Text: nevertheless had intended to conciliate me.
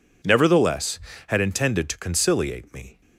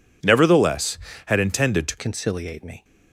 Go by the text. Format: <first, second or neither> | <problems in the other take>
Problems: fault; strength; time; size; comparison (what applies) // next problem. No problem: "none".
first | changes voice at "conciliate"; from 1.9 s on; 0.9 s long